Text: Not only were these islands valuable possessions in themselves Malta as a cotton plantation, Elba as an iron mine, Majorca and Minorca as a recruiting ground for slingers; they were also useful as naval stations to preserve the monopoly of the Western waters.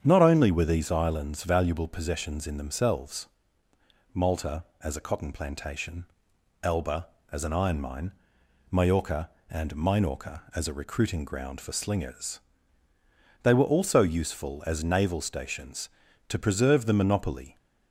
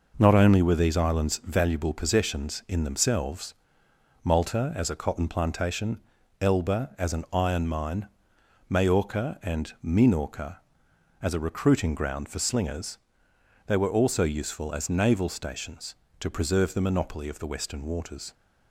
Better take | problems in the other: second | starts louder than the rest; strong; until 1.0 s; 8 dB // pauses between "themselves" and "Malta"; noticeable; at 3.2 s; 0.86 s long; noticeable in the second // stops before "of the Western waters"; at 17.5 s

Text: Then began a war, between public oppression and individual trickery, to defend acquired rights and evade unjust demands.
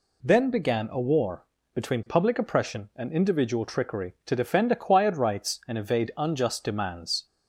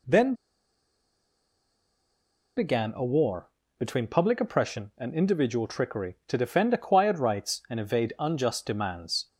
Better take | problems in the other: first | pauses between "Then" and "began"; strong; at 0.3 s; 2.2 s long

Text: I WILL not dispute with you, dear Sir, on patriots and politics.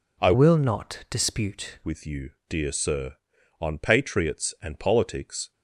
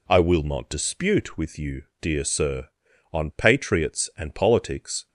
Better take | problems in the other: second | changes voice from "WILL" to "dispute"; from 0.3 to 1.7 s; 1.4 s long

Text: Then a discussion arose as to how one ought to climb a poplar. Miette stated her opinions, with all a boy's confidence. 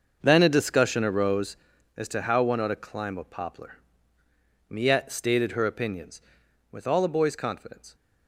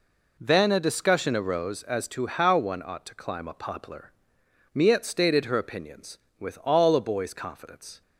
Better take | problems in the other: second | starts louder than the rest; noticeable; until 1.7 s; 6 dB

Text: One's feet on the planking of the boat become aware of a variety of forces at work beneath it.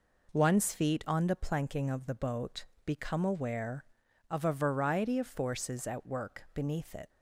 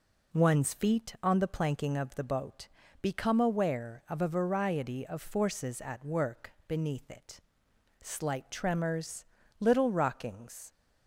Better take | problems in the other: first | pauses between "boat" and "become"; slight; at 2.6 s; 0.34 s long; slight in the first // goes on to say "Slight tremors little rockings"; strong; from 7.9 s on; 2.7 s long

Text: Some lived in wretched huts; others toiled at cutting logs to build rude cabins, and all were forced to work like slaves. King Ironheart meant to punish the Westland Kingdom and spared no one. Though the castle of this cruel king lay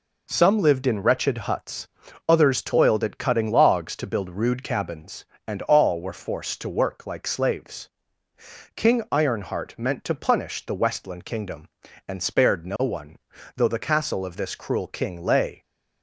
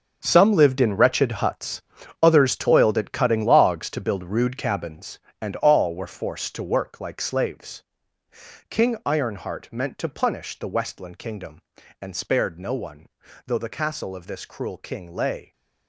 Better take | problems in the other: first | gets quieter; strong; throughout; 12 dB

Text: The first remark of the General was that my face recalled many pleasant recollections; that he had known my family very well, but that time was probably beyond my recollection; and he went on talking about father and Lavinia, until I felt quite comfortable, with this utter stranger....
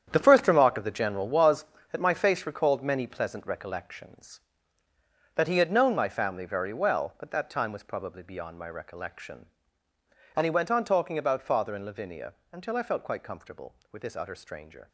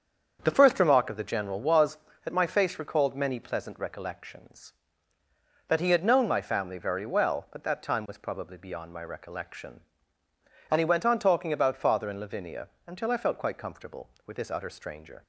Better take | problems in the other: second | gets quieter; strong; throughout; 11 dB // starts louder than the rest; strong; until 1.1 s; 9 dB; strong in the second

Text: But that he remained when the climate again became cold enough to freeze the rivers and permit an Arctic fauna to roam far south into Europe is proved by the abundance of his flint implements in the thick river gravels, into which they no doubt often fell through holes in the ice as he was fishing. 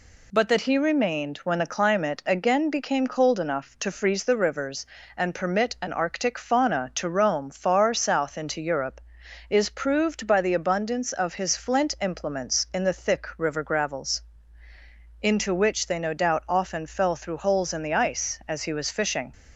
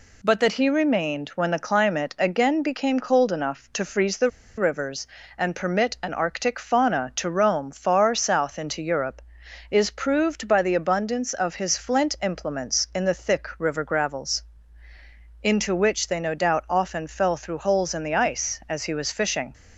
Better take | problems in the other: first | pauses between "the" and "rivers"; slight; at 4.2 s; 0.28 s long

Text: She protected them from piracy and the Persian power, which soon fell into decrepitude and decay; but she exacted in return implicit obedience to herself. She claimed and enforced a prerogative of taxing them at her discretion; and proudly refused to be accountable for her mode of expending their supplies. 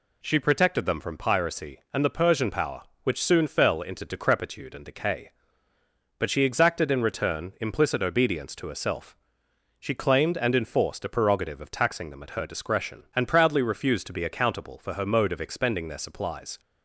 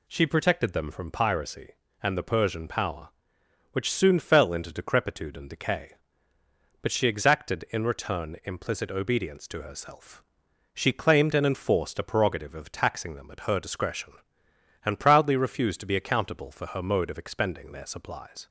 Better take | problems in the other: neither | none

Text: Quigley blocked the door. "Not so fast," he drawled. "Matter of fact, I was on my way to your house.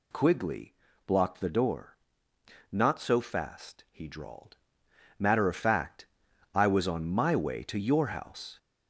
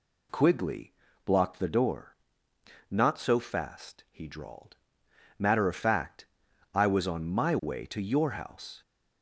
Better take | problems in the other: second | gets louder; noticeable; throughout; 4.5 dB // pauses between "Quigley" and "blocked"; slight; at 0.7 s; 0.32 s long; slight in the second

